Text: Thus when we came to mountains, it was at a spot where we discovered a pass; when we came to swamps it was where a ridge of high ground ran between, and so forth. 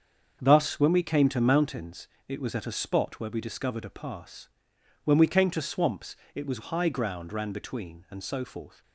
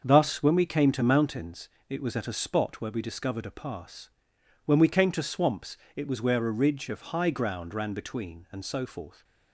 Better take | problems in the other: second | starts louder than the rest; until 1.4 s; 7 dB; also in the second // pauses between "swamps" and "it"; slight; at 6.1 s; 0.20 s long; slight in the second // skips "where a ridge of"; at 6.6 s

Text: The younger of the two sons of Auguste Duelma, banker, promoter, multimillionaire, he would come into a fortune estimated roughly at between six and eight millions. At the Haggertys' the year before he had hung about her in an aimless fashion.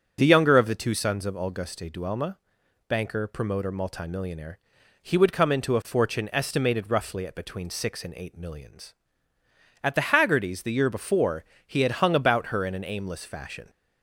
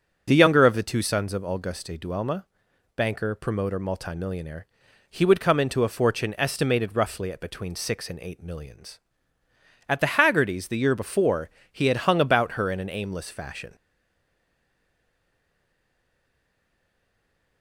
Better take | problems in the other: first | starts louder than the rest; noticeable; until 1.3 s; 6 dB; also in the first // pauses between "before" and "he"; slight; at 11.4 s; 0.22 s long; slight in the first // stays silent after the last word; strong; from 13.7 s on; 3.9 s long

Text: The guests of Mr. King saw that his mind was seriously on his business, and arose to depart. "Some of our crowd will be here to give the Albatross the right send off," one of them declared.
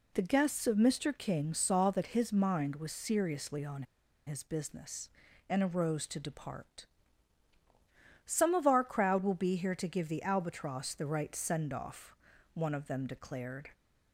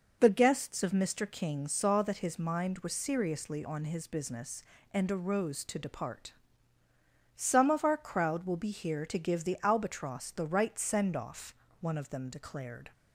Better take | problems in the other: second | pauses between "on" and "his"; at 3.8 s; 0.43 s long

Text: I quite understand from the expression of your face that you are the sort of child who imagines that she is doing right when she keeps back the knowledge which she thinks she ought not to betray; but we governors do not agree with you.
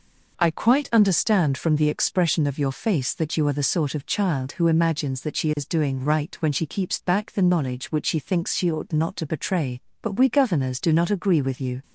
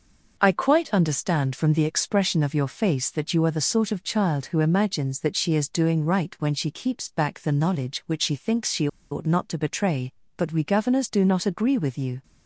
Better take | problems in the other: first | starts louder than the rest; noticeable; until 1.3 s; 6 dB // pauses between "she" and "ought"; slight; at 8.8 s; 0.24 s long

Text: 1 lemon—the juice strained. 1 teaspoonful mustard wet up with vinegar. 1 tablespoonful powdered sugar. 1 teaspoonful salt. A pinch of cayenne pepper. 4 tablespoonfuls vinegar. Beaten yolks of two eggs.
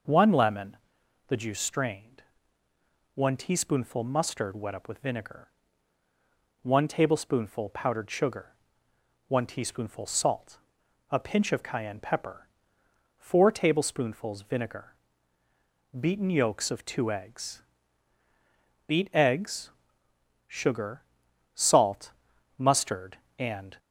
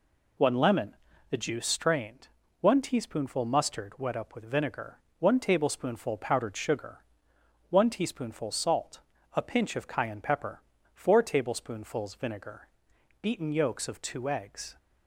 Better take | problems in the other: second | goes on to say "Beat eggs sugar salt mustard and"; strong; from 18.8 s on; 4.9 s long

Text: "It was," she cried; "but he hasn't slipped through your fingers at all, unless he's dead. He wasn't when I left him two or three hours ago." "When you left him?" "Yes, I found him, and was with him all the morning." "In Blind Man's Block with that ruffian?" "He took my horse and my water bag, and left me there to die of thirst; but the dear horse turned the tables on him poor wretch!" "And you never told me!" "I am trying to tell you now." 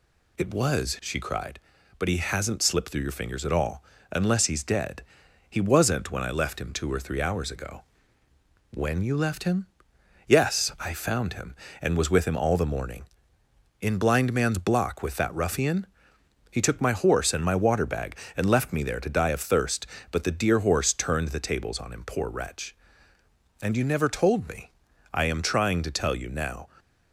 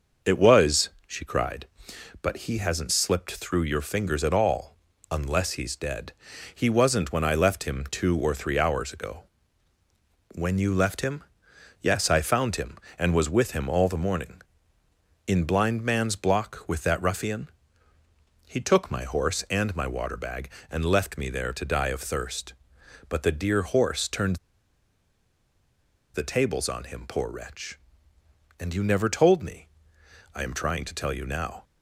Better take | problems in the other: first | starts louder than the rest; noticeable; until 1.4 s; 6 dB // pauses between "turned" and "the"; strong; at 24.3 s; 1.7 s long

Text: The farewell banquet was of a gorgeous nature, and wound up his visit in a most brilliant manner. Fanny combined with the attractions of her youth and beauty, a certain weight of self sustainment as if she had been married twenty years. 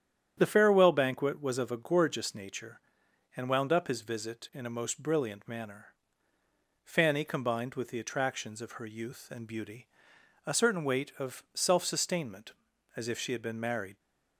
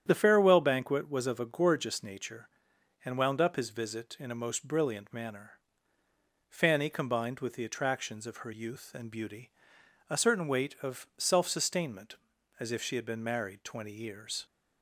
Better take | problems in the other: second | starts louder than the rest; strong; until 1.3 s; 9.5 dB; strong in the second // stops before "twenty years"; at 13.9 s

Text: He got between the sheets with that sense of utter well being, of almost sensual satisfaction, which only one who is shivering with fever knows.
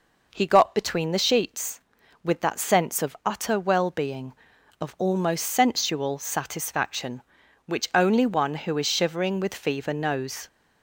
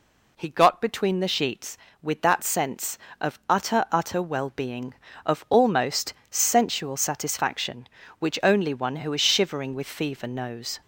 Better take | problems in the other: first | says "utter" twice; at 3.8 s // pauses between "almost" and "sensual"; slight; at 6.1 s; 0.16 s long

